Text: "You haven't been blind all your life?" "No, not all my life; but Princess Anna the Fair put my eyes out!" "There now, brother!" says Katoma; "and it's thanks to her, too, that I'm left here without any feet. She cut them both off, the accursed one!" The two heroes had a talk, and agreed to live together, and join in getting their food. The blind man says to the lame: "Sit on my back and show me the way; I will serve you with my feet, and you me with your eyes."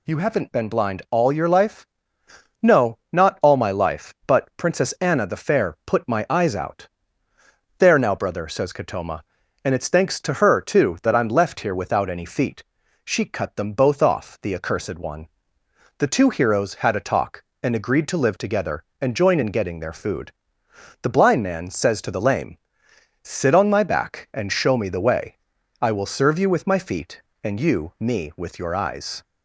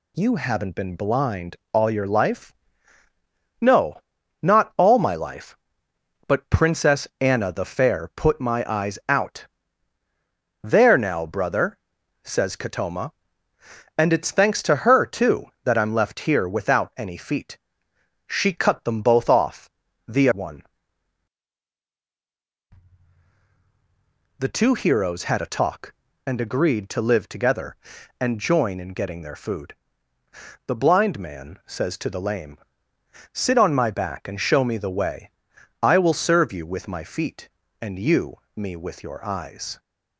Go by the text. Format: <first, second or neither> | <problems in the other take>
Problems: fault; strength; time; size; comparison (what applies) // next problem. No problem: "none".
first | pauses between "blind" and "all"; slight; at 1.5 s; 0.16 s long // skips "accursed"; at 20.3 s // pauses between "you" and "me"; slight; at 38.3 s; 0.16 s long